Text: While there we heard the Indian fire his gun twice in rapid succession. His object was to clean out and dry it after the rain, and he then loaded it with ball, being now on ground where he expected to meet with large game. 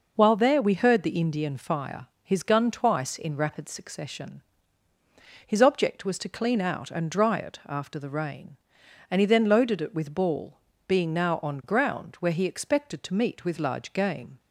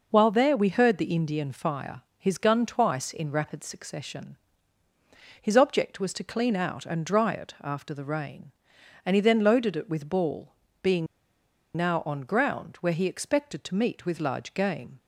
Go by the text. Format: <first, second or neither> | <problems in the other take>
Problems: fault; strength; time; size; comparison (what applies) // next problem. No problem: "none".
first | pauses between "fire" and "his"; slight; at 2.0 s; 0.16 s long; slight in the first // pauses between "being" and "now"; noticeable; at 11.0 s; 0.69 s long